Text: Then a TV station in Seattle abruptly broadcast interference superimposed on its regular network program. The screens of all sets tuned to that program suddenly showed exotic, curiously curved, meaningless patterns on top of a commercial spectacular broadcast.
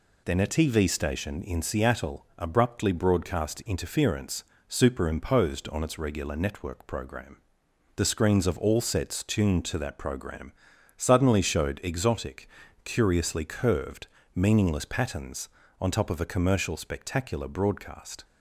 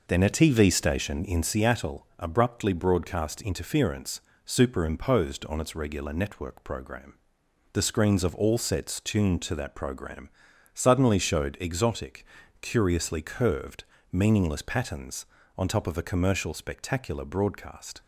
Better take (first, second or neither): first